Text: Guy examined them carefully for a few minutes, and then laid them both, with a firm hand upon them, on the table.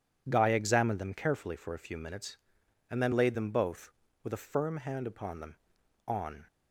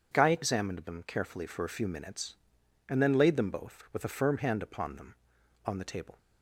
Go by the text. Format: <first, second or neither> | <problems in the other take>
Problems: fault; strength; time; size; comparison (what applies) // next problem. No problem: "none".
second | stops before "the table"; at 6.4 s